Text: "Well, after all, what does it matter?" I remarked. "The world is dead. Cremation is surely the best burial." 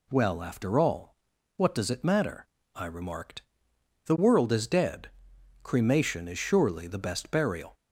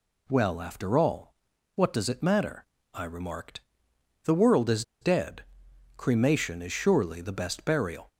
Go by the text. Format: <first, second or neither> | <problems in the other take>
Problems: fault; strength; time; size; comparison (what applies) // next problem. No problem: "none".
first | pauses between "is" and "dead"; slight; at 4.8 s; 0.18 s long